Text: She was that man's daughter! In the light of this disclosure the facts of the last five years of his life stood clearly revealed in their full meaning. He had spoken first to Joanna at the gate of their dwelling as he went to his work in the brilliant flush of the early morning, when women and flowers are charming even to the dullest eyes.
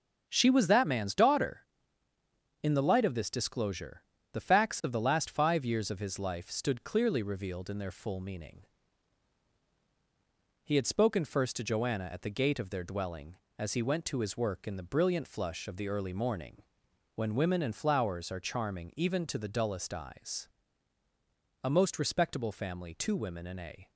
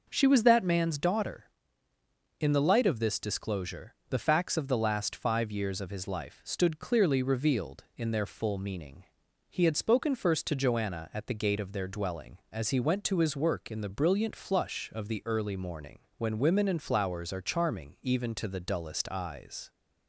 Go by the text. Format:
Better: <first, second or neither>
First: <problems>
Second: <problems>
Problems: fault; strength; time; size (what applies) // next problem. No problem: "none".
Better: second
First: starts louder than the rest; strong; until 1.3 s; 7.5 dB // pauses between "disclosure" and "the"; slight; at 4.0 s; 0.30 s long // goes on to say "A most respectable family two women and a"; strong; from 21.6 s on; 2.2 s long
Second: pauses between "disclosure" and "the"; slight; at 3.9 s; 0.16 s long